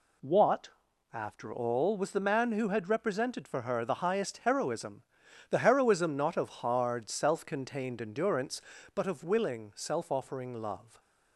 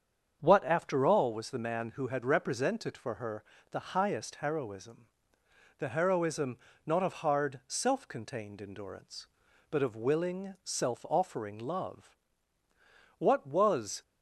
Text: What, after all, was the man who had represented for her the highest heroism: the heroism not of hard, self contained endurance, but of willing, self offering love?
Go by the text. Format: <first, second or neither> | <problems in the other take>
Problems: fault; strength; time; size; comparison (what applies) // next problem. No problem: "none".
first | starts louder than the rest; strong; until 1.4 s; 7.5 dB // pauses between "her" and "the"; slight; at 3.4 s; 0.28 s long // pauses between "heroism" and "not"; slight; at 6.5 s; 0.30 s long // goes on to say "What was"; noticeable; from 13.1 s on; 0.84 s long